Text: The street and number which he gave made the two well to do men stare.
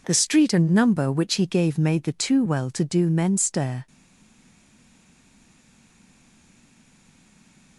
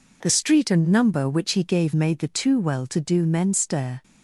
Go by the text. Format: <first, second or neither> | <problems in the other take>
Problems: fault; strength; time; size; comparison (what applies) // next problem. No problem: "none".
second | stays silent after the last word; strong; from 3.8 s on; 3.9 s long